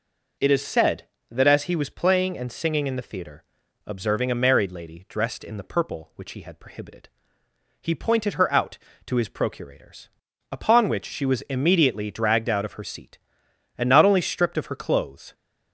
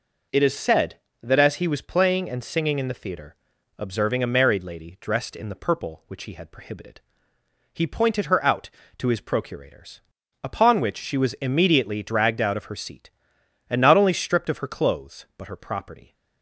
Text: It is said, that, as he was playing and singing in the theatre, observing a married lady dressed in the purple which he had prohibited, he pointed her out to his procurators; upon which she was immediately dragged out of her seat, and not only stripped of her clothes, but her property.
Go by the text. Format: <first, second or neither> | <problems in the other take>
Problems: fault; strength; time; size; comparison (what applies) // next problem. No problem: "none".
second | stops before "but her property"; at 15.3 s